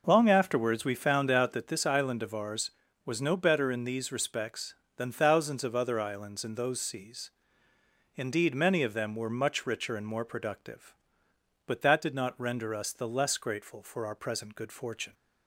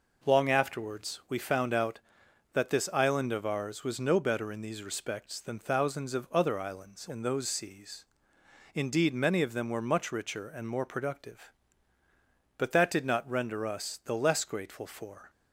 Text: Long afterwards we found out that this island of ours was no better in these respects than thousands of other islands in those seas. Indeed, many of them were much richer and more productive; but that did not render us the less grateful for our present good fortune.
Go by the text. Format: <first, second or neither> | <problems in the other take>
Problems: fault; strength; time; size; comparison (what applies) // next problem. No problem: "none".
first | stops before "our present good fortune"; at 15.2 s